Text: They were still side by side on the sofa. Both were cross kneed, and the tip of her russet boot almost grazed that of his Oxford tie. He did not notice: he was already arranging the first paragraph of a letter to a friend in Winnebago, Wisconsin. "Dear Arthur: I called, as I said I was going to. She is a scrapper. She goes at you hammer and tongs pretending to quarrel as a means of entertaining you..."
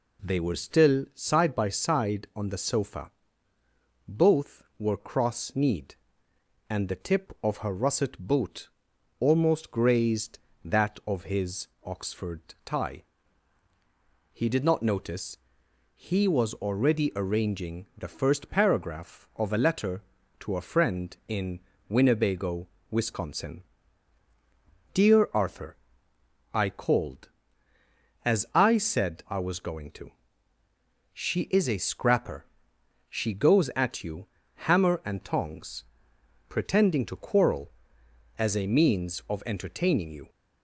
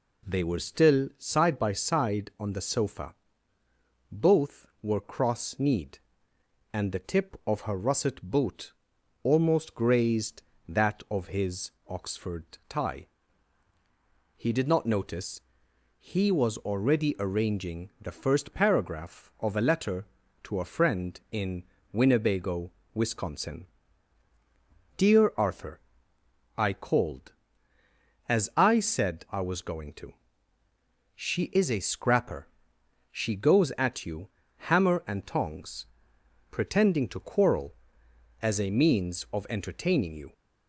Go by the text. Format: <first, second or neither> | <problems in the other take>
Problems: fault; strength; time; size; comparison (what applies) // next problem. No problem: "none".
neither | pauses between "boot" and "almost"; noticeable; the same in both // pauses between "his" and "Oxford"; slight; the same in both // pauses between "Oxford" and "tie"; slight; the same in both // pauses between "in" and "Winnebago"; slight; the same in both // pauses between "you" and "hammer"; the same in both // pauses between "tongs" and "pretending"; noticeable; the same in both